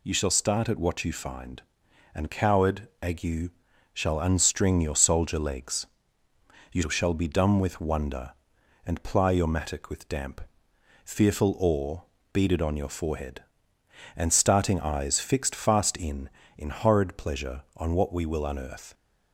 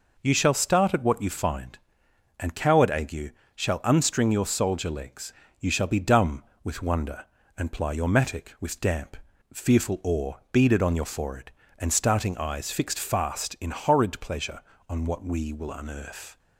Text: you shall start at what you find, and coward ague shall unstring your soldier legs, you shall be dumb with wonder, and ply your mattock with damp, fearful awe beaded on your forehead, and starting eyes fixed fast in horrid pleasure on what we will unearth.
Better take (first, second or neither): second